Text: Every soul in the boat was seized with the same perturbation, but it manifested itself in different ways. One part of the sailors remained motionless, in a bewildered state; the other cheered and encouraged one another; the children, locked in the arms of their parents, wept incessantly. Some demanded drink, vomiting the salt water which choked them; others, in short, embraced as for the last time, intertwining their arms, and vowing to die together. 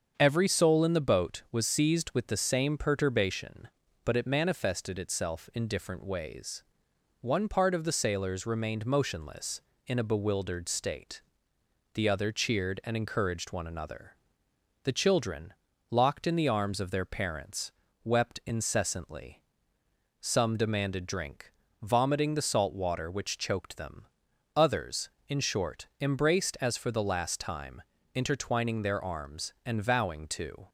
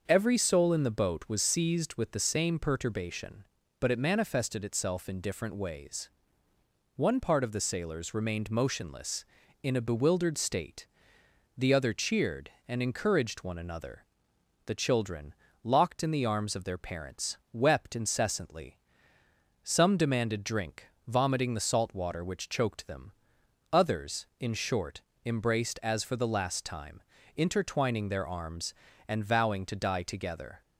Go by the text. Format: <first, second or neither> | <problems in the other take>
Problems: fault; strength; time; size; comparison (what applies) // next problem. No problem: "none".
second | starts louder than the rest; until 1.1 s; 7 dB; also in the second // stops before "die together"; at 30.6 s